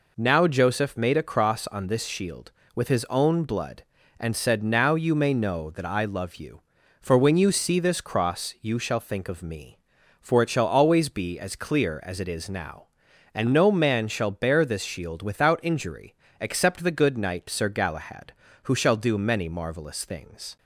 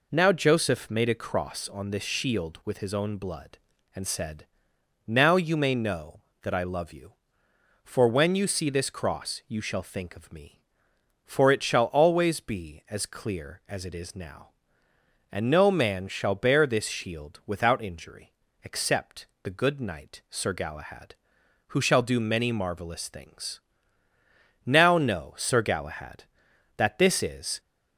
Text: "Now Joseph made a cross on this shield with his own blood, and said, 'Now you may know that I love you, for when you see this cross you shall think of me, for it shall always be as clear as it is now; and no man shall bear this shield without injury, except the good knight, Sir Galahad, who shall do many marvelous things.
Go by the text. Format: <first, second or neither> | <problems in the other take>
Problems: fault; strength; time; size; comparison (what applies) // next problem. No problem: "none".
first | pauses between "except" and "the"; slight; at 19.2 s; 0.18 s long // goes on to say "Now know Sir Galahad that this is"; strong; from 24.6 s on; 2.9 s long